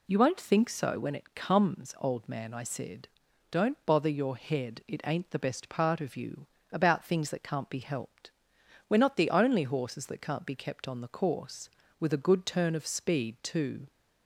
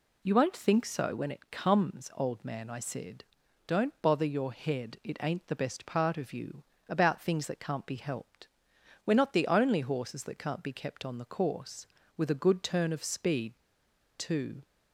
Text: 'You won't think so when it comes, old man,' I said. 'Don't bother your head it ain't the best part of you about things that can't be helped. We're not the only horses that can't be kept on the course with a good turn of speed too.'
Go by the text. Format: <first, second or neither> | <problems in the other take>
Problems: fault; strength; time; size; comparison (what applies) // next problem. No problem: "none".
first | pauses between "you" and "about"; slight; at 6.6 s; 0.26 s long; slight in the first // pauses between "speed" and "too"; noticeable; at 13.5 s; 0.60 s long